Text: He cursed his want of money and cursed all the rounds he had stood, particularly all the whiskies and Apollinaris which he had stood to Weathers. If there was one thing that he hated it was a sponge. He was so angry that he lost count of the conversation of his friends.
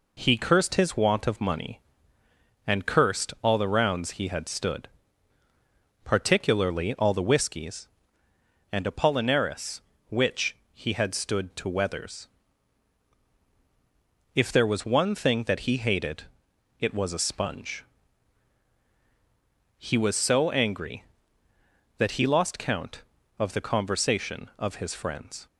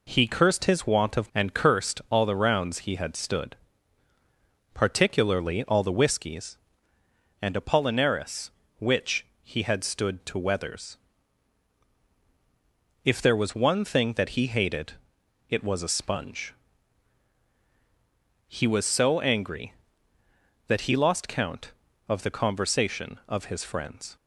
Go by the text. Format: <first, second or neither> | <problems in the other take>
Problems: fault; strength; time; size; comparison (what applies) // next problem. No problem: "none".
first | skips "money"; at 1.3 s // pauses between "which" and "he"; slight; at 9.2 s; 0.16 s long; slight in the first // pauses between "hated" and "it"; noticeable; at 14.9 s; 0.58 s long; noticeable in the first